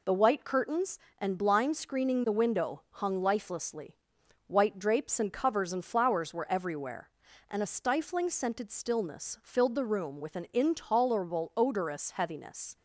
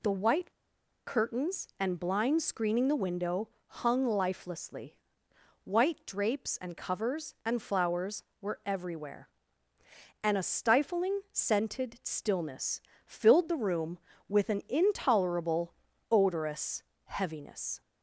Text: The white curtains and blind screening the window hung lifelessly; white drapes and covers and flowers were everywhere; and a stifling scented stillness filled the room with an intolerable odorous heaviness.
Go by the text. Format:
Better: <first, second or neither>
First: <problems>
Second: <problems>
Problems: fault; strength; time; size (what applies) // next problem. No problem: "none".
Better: first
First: none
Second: pauses between "white" and "curtains"; noticeable; at 0.5 s; 0.54 s long // pauses between "window" and "hung"; slight; at 3.4 s; 0.18 s long // pauses between "stillness" and "filled"; slight; at 12.8 s; 0.24 s long // pauses between "intolerable" and "odorous"; slight; at 15.7 s; 0.34 s long // pauses between "odorous" and "heaviness"; slight; at 16.8 s; 0.22 s long